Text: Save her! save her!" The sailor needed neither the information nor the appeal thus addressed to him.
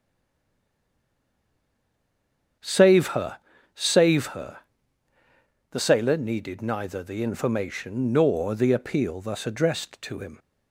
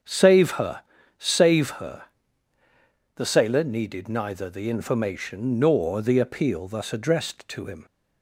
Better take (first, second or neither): second